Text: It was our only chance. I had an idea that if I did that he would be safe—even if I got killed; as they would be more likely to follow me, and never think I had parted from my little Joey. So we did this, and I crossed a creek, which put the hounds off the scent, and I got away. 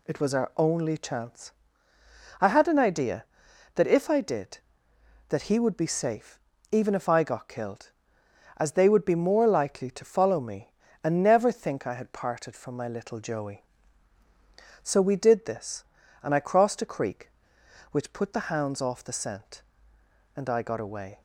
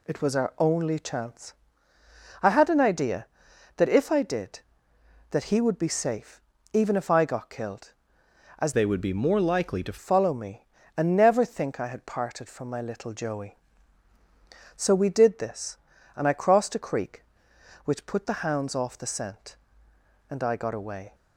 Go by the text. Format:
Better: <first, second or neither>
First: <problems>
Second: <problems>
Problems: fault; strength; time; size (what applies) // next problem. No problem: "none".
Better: first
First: none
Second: changes voice from "they" to "to"; from 8.7 to 9.9 s; 1.2 s long